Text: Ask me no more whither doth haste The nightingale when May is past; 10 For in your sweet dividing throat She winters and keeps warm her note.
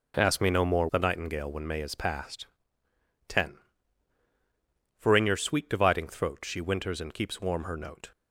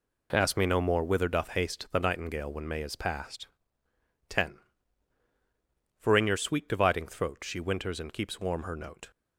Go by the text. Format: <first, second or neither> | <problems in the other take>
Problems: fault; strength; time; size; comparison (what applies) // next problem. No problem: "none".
second | skips "whither doth haste"; at 0.8 s